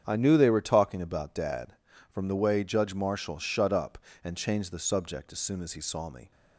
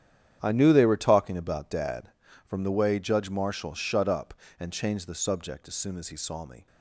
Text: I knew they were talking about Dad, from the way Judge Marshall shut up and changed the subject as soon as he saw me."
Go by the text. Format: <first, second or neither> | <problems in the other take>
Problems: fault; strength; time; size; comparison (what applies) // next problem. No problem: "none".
first | gets quieter; strong; throughout; 12.5 dB // starts louder than the rest; strong; until 1.4 s; 9.5 dB; strong in the first